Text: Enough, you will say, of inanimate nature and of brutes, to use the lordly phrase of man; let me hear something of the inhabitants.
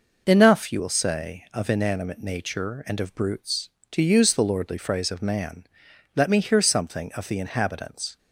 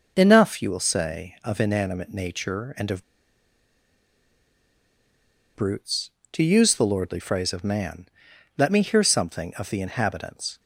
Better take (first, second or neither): first